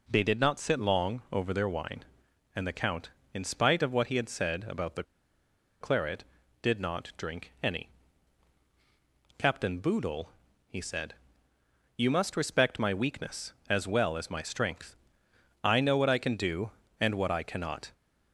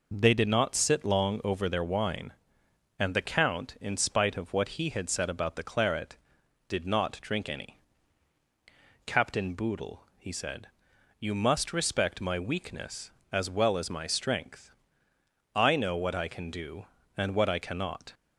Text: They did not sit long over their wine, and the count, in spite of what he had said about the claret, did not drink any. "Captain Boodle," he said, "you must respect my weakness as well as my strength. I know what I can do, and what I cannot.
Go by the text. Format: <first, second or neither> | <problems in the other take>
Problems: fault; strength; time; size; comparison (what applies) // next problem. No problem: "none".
second | pauses between "the" and "claret"; noticeable; at 5.0 s; 0.77 s long